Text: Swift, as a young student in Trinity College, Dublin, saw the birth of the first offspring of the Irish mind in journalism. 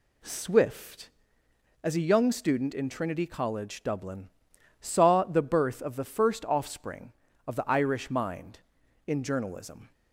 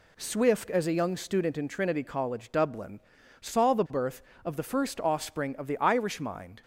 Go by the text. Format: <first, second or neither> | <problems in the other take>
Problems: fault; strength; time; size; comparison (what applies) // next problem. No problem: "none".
first | stops before "in journalism"; at 6.6 s